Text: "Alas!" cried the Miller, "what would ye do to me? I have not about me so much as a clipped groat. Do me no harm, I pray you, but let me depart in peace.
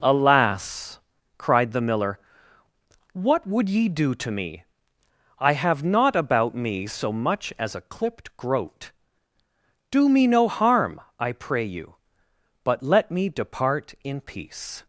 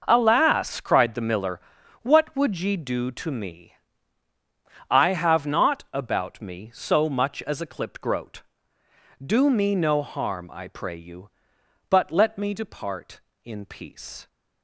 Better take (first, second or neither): neither